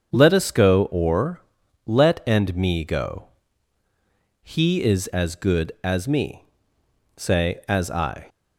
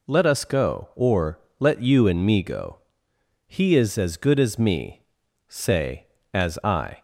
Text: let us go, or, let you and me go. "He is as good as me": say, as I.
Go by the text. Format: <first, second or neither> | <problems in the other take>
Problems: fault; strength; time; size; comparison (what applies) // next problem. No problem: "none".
second | starts louder than the rest; until 1.1 s; 7 dB // skips "you"; at 2.2 s